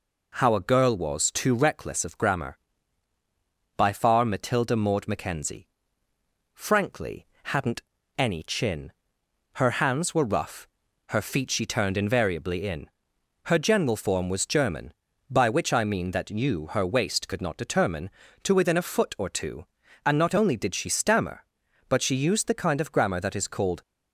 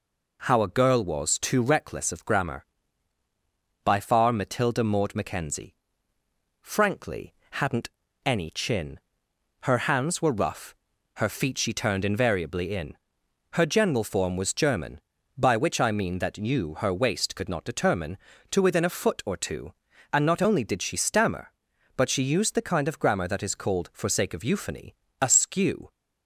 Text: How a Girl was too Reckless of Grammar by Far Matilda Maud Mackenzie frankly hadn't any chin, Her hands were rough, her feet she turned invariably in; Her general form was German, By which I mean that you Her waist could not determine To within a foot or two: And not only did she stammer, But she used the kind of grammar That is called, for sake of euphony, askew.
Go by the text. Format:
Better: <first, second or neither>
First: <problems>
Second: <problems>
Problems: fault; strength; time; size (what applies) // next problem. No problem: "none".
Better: second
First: pauses between "Mackenzie" and "frankly"; noticeable; at 5.6 s; 0.88 s long // pauses between "frankly" and "hadn't"; slight; at 7.2 s; 0.16 s long // pauses between "hadn't" and "any"; slight; at 7.8 s; 0.34 s long // stops before "for sake of euphony askew"; at 23.8 s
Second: pauses between "Mackenzie" and "frankly"; noticeable; at 5.7 s; 0.88 s long // pauses between "frankly" and "hadn't"; slight; at 7.3 s; 0.16 s long // pauses between "hadn't" and "any"; slight; at 7.9 s; 0.34 s long